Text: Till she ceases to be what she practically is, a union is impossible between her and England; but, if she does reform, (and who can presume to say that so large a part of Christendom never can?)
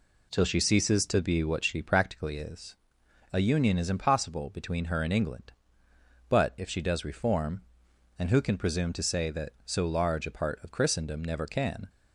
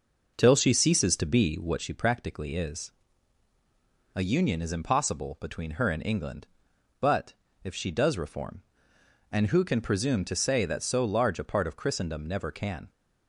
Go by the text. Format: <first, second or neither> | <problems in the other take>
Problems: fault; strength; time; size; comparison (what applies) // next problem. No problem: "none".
first | starts louder than the rest; noticeable; until 1.9 s; 5.5 dB